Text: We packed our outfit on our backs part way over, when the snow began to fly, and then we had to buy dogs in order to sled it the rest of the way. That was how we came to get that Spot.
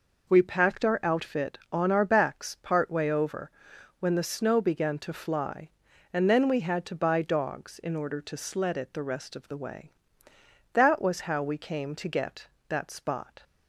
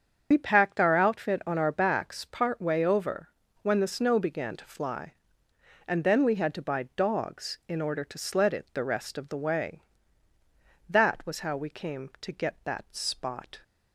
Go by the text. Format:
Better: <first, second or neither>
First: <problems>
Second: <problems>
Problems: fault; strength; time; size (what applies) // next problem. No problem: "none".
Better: first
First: none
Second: loses the start of "We"; at 0.3 s; 60 ms // starts louder than the rest; until 1.3 s; 7 dB